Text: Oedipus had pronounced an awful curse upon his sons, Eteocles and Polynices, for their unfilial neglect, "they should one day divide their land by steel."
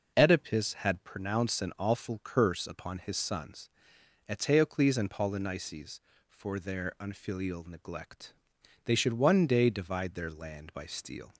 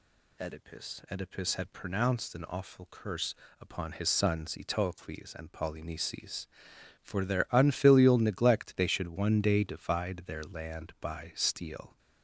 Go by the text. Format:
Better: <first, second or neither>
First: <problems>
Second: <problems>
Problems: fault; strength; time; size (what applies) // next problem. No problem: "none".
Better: first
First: none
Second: says "Oedipus" twice; at 1.0 s // pauses between "curse" and "upon"; slight; at 3.3 s; 0.26 s long